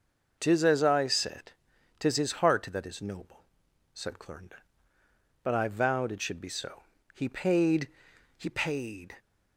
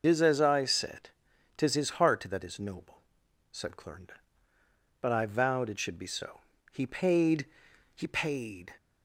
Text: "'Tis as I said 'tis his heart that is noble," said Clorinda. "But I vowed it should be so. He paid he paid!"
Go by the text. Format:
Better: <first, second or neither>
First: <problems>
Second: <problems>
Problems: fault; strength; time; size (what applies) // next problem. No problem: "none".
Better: first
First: pauses between "said" and "tis"; noticeable; at 1.5 s; 0.48 s long // pauses between "paid" and "he"; noticeable; at 7.8 s; 0.50 s long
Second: loses the start of "Tis"; at 0.0 s; 65 ms // pauses between "said" and "tis"; noticeable; at 1.0 s; 0.48 s long // pauses between "paid" and "he"; noticeable; at 7.4 s; 0.50 s long